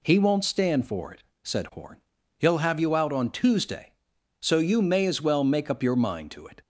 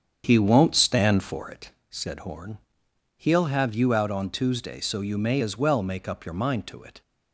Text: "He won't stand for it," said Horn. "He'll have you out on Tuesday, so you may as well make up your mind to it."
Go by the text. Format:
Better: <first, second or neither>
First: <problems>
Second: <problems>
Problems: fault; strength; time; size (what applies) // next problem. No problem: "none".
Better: first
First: none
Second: starts louder than the rest; strong; until 1.8 s; 8 dB